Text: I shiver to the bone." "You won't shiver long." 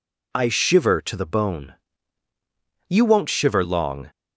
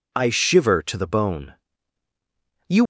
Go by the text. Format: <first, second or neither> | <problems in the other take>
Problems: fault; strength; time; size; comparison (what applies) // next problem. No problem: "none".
first | stops before "won't shiver long"; at 2.8 s